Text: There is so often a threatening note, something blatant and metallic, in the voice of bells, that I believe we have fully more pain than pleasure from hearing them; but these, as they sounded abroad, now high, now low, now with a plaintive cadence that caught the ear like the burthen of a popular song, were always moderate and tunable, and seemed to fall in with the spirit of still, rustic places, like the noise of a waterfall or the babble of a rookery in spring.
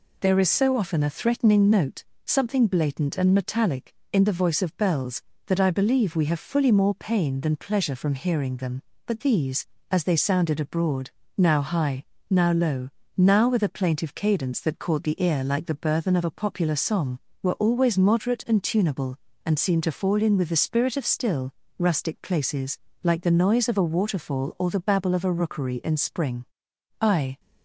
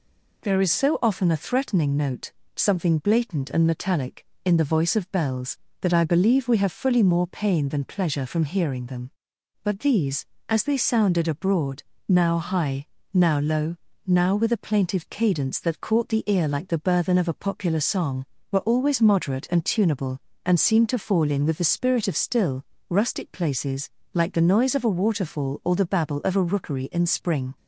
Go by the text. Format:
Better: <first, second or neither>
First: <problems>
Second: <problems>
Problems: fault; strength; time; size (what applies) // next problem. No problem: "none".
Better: second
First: goes on to say "I"; slight; from 26.9 s on; 0.40 s long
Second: none